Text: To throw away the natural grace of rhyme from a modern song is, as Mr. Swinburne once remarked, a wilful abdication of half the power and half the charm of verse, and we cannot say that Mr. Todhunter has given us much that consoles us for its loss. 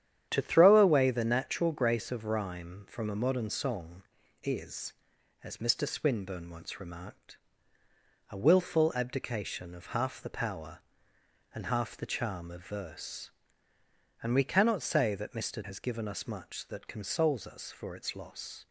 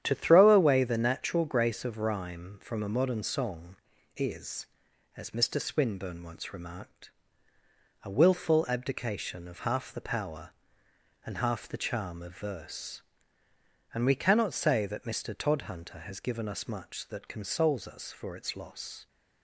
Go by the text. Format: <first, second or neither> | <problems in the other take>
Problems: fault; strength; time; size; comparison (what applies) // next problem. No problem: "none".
second | starts louder than the rest; strong; until 1.3 s; 10 dB; strong in the second // skips "Todhunter"; at 15.6 s